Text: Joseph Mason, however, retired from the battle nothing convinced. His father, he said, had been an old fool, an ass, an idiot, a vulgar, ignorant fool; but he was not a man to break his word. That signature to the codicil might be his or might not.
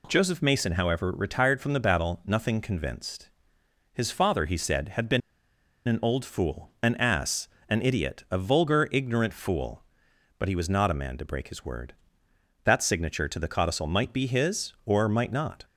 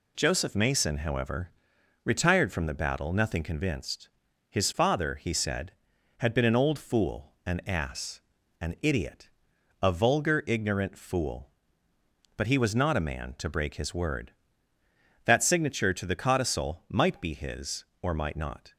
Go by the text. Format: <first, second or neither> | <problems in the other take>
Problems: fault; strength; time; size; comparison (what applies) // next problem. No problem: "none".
second | pauses between "been" and "an"; noticeable; at 5.2 s; 0.68 s long